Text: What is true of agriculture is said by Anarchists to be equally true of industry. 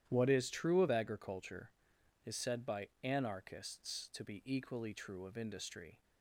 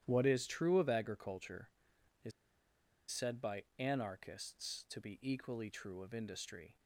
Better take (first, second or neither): first